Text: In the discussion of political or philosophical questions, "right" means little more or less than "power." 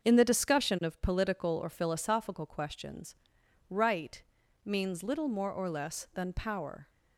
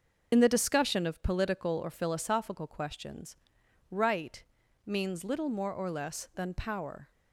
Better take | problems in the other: first | loses the start of "In"; at 0.3 s; 50 ms // starts louder than the rest; until 1.3 s; 6 dB; also in the first // pauses between "right" and "means"; at 4.4 s; 0.44 s long; also in the first

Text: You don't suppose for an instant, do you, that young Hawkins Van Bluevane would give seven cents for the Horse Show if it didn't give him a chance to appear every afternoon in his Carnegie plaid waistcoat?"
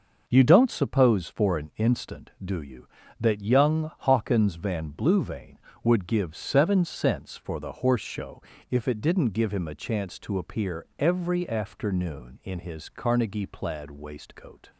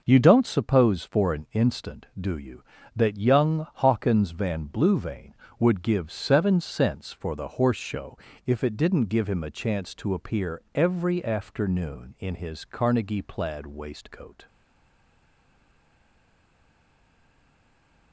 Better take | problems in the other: first | pauses between "Show" and "if"; slight; at 8.1 s; 0.26 s long; slight in the first // stays silent after the last word; strong; from 14.4 s on; 3.7 s long

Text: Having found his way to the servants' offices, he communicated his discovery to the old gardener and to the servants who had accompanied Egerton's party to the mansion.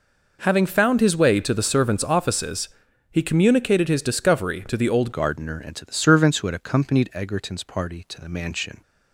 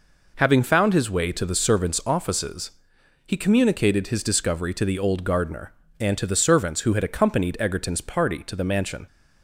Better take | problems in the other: second | changes voice at "gardener"; from 5.1 s on; 3.7 s long

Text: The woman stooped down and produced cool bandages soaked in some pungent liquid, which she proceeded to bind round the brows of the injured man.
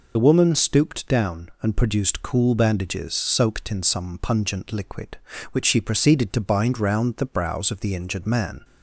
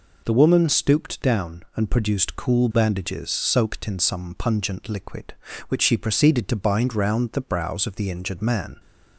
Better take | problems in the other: second | loses the start of "The"; at 0.1 s; 40 ms

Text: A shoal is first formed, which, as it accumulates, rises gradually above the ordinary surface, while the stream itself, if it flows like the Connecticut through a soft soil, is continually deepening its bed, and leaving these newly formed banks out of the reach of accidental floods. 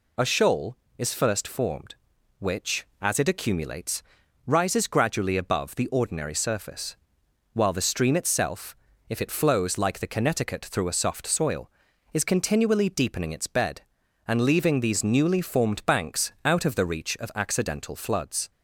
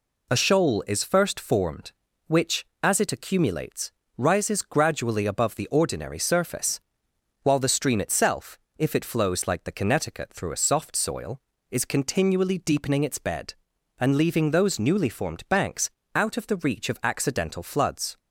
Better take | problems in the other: first | says "those" for "these"; at 14.4 s // pauses between "banks" and "out"; slight; at 15.8 s; 0.26 s long

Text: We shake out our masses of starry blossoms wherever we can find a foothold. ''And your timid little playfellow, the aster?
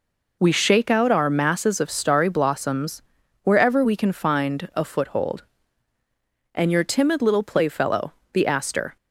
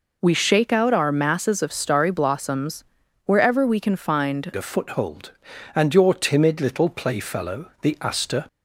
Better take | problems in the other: first | pauses between "blossoms" and "wherever"; at 2.8 s; 0.40 s long; also in the first // changes voice at "a"; from 4.5 s on; 3.9 s long

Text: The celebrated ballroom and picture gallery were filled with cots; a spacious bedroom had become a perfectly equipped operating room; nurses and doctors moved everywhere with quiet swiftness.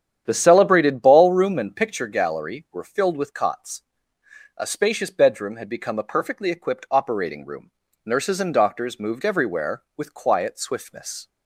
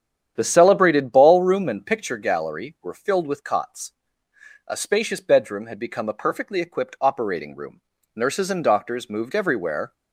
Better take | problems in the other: first | starts louder than the rest; strong; until 1.3 s; 9 dB; strong in the first // stops before "with quiet swiftness"; at 9.9 s

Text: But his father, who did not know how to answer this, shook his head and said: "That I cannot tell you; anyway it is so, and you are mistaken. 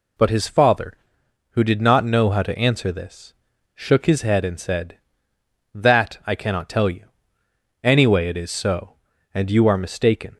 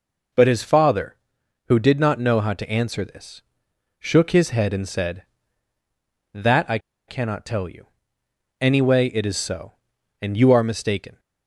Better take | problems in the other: first | pauses between "I" and "cannot"; slight; at 6.7 s; 0.29 s long

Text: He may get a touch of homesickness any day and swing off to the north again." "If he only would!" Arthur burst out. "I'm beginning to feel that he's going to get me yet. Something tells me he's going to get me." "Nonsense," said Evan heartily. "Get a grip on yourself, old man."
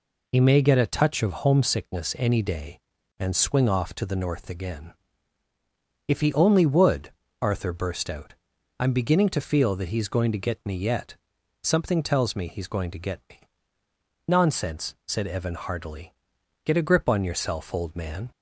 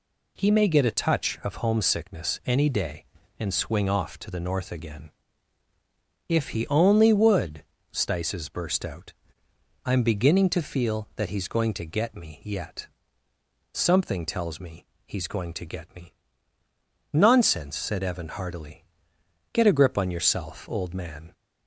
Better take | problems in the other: first | says "Stices" for "Arthur"; at 7.9 s // pauses between "me" and "he's"; slight; at 14.8 s; 0.22 s long

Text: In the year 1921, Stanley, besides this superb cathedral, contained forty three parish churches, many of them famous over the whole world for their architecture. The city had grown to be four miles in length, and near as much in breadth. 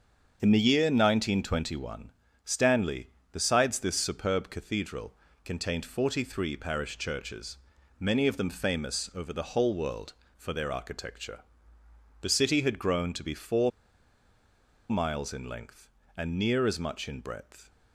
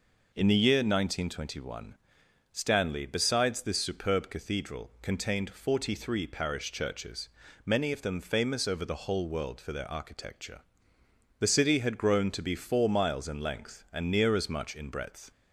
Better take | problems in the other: second | starts louder than the rest; until 1.4 s; 6.5 dB // pauses between "four" and "miles"; at 13.6 s; 1.1 s long

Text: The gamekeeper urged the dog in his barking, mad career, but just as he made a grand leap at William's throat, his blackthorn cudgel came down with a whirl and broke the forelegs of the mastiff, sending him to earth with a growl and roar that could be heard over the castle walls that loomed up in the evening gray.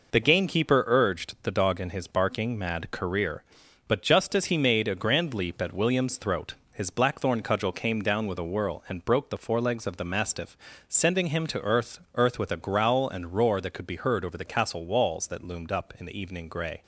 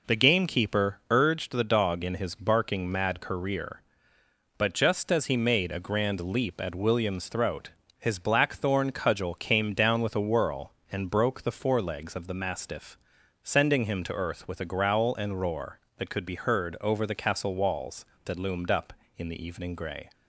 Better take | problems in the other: second | says "earth" twice; at 12.1 s

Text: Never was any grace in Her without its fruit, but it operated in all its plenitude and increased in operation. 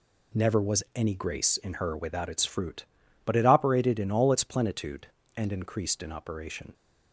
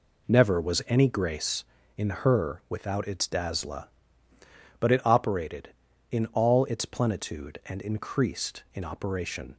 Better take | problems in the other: first | says "dazzla" for "fruit"; at 3.2 s

